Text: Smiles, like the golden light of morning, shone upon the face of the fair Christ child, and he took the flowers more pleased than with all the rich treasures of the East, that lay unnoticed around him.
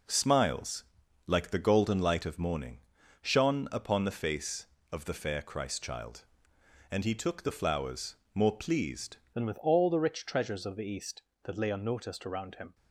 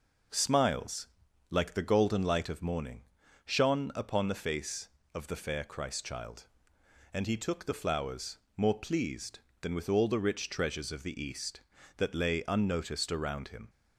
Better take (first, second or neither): second